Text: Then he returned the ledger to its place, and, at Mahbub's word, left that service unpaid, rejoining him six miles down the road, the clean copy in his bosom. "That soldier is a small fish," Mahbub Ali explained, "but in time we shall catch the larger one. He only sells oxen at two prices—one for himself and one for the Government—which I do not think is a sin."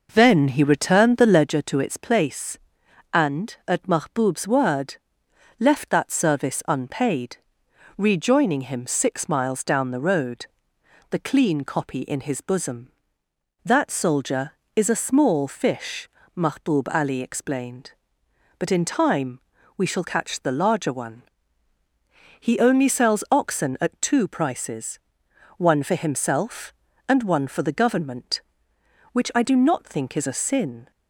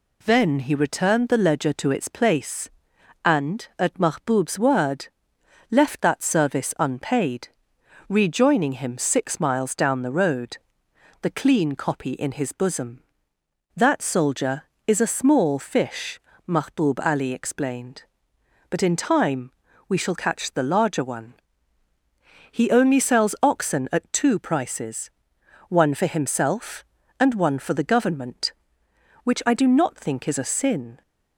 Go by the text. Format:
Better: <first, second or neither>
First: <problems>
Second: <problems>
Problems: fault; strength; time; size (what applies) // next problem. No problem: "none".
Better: second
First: starts louder than the rest; noticeable; until 1.6 s; 5.5 dB // pauses between "time" and "we"; at 19.3 s; 0.38 s long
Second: pauses between "time" and "we"; at 19.4 s; 0.38 s long